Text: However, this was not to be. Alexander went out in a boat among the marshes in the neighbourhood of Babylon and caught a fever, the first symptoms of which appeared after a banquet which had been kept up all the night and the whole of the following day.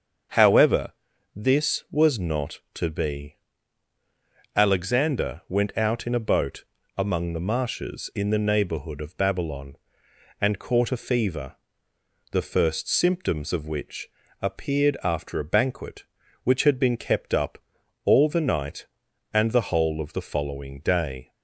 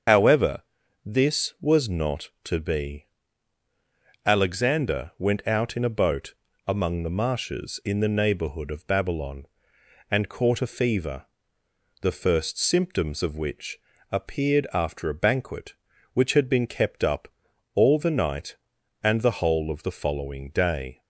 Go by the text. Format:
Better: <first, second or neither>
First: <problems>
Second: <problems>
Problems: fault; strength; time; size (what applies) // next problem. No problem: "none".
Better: first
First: starts louder than the rest; until 1.7 s; 7 dB // pauses between "boat" and "among"; slight; at 6.6 s; 0.32 s long // pauses between "which" and "appeared"; slight; at 14.0 s; 0.32 s long // pauses between "up" and "all"; noticeable; at 17.5 s; 0.48 s long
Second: loses the start of "However"; at 0.0 s; 60 ms // starts louder than the rest; until 1.5 s; 7 dB // pauses between "boat" and "among"; slight; at 6.3 s; 0.32 s long // pauses between "which" and "appeared"; slight; at 13.7 s; 0.32 s long // pauses between "up" and "all"; noticeable; at 17.2 s; 0.48 s long